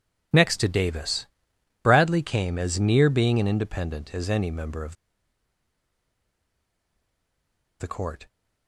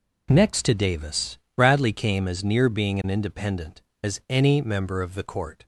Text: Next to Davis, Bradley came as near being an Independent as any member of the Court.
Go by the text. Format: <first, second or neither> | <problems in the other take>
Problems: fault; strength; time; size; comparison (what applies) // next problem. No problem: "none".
second | pauses between "of" and "the"; strong; at 4.9 s; 2.8 s long